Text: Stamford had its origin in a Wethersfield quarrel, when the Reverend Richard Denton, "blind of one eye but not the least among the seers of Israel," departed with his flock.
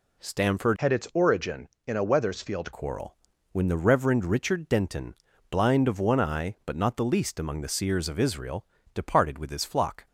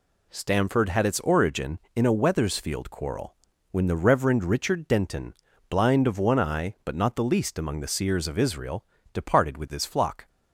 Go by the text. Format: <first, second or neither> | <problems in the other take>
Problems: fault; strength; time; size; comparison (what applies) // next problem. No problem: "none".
second | changes voice from "had" to "Wethersfield"; from 0.7 to 2.7 s; 2.0 s long